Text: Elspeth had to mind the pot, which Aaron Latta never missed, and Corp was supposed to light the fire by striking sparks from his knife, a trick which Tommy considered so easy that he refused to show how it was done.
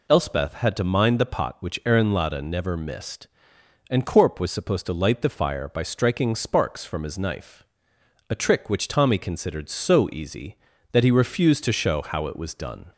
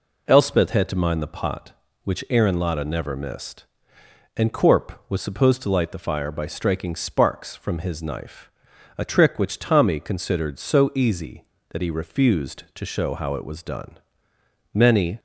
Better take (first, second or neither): first